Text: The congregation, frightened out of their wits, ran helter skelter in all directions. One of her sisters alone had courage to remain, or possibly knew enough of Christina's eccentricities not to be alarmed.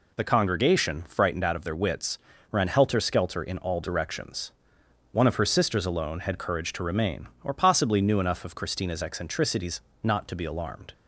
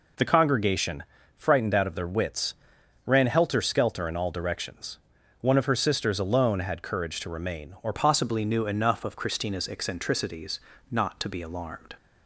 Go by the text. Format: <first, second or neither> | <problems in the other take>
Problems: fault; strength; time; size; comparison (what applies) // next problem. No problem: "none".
first | changes voice at "possibly"; from 7.9 s on; 4.0 s long // pauses between "eccentricities" and "not"; slight; at 10.6 s; 0.28 s long; slight in the first